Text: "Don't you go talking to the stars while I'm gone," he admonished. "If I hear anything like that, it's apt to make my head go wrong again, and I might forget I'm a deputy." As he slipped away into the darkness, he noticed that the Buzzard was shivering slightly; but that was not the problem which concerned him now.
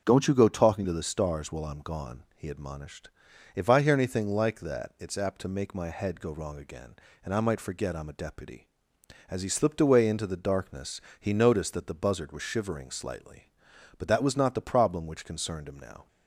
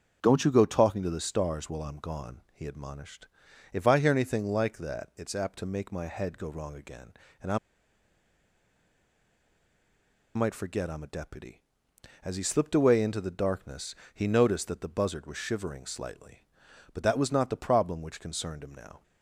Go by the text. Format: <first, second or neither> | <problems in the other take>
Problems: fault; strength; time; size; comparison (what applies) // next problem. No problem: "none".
first | starts louder than the rest; until 1.2 s; 6.5 dB; also in the first // pauses between "I" and "might"; strong; at 7.5 s; 2.7 s long